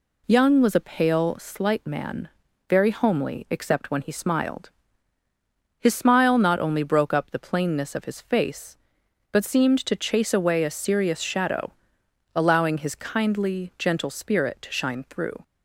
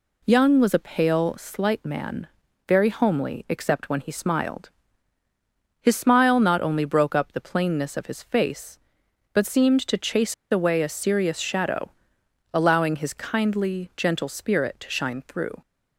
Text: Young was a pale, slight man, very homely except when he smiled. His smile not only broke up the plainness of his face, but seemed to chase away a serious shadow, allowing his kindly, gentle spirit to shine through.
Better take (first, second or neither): first